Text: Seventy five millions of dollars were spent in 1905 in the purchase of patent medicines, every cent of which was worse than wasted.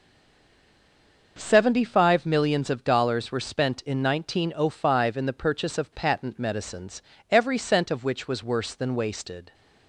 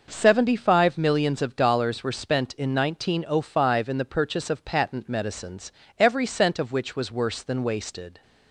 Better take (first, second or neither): second